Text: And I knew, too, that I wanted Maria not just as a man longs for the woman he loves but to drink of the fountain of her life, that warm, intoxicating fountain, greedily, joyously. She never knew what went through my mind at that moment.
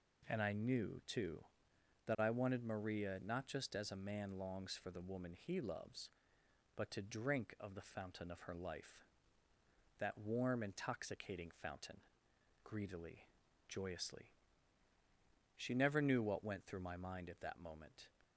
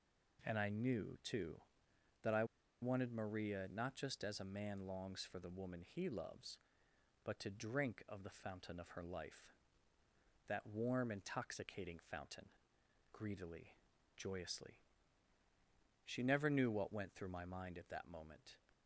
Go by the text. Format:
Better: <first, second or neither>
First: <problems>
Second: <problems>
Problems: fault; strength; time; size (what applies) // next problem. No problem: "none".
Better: first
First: none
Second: pauses between "I" and "wanted"; at 2.4 s; 0.37 s long